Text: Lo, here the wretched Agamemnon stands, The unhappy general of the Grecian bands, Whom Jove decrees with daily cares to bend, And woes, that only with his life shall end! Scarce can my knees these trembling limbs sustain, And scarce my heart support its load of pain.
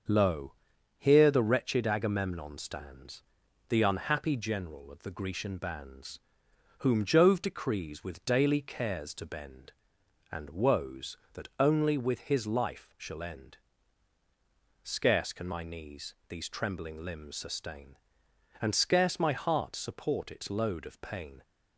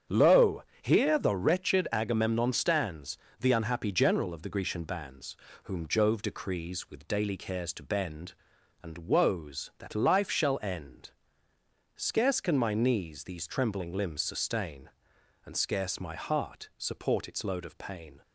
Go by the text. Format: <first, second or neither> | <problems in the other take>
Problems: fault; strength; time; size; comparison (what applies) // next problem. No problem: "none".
first | starts louder than the rest; strong; until 1.3 s; 8 dB; also in the first // skips "only with his"; at 9.9 s